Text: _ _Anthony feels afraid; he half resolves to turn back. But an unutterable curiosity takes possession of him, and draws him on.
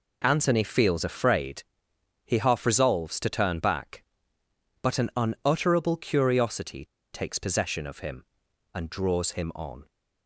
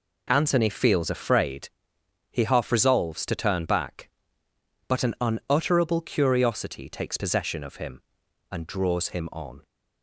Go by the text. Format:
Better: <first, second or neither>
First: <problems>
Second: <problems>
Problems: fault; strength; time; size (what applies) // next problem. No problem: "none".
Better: second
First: pauses between "curiosity" and "takes"; slight; at 6.8 s; 0.27 s long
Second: none